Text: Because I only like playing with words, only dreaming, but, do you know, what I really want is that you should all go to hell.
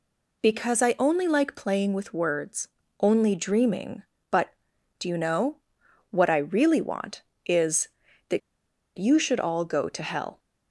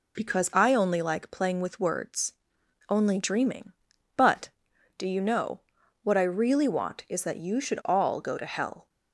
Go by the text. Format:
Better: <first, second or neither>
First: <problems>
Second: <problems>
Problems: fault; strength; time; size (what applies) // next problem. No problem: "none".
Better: second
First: pauses between "that" and "you"; noticeable; at 8.4 s; 0.58 s long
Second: none